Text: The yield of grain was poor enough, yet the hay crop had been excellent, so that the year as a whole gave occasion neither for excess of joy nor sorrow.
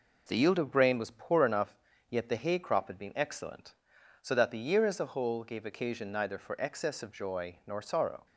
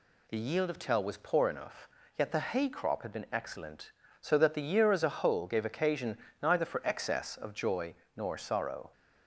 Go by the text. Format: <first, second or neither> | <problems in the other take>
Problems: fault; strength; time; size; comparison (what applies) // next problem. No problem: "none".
first | says "tell" for "grain"; at 0.7 s // pauses between "occasion" and "neither"; slight; at 6.1 s; 0.24 s long // pauses between "joy" and "nor"; slight; at 7.9 s; 0.24 s long